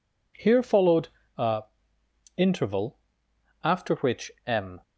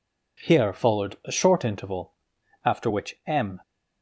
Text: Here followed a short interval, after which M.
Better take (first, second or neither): second